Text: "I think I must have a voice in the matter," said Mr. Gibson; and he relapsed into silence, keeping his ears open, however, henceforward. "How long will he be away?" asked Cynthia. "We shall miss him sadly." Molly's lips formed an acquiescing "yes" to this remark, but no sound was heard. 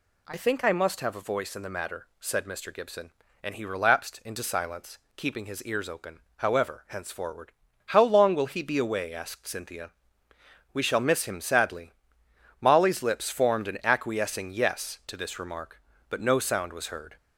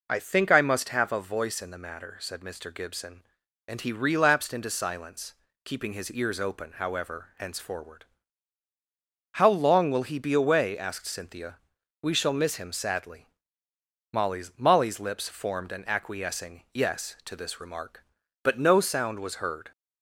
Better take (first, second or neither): first